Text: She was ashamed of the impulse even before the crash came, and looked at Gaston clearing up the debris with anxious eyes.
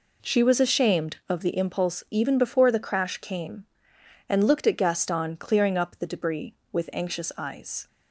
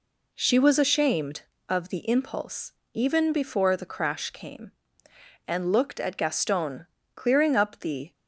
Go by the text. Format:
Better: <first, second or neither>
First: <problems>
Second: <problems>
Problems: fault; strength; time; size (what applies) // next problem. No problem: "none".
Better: first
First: none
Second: pauses between "impulse" and "even"; slight; at 2.7 s; 0.20 s long // pauses between "Gaston" and "clearing"; slight; at 6.8 s; 0.28 s long // stops before "debris with anxious eyes"; at 8.1 s